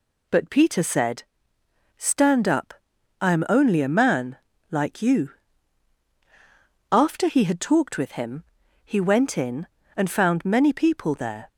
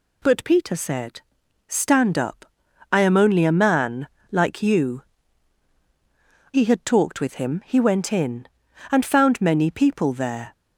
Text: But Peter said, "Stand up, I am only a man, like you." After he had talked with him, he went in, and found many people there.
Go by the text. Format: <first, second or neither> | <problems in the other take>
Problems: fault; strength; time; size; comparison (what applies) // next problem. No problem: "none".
first | skips "After"; at 5.7 s